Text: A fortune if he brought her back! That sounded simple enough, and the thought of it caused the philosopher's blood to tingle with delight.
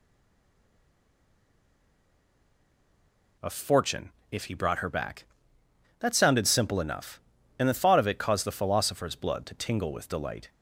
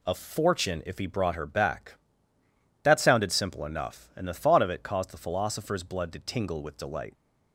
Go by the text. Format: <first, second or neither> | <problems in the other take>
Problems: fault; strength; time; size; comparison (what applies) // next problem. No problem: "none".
second | stays silent before the first word; strong; until 3.3 s; 3.3 s long // pauses between "fortune" and "if"; slight; at 4.0 s; 0.22 s long